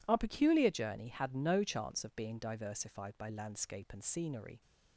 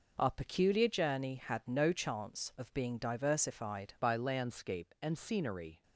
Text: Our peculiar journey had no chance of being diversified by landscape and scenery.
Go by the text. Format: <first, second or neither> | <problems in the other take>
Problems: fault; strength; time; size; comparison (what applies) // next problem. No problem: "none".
first | changes voice at "by"; from 4.0 s on; 1.8 s long